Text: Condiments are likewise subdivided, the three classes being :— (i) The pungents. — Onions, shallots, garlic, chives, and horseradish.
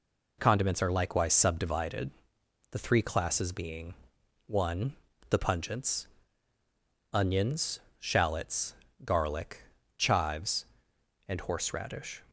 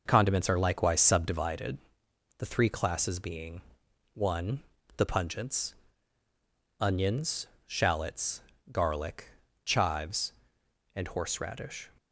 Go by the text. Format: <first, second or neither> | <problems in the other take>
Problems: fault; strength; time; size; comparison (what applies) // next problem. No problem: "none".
first | starts louder than the rest; noticeable; until 1.4 s; 5.5 dB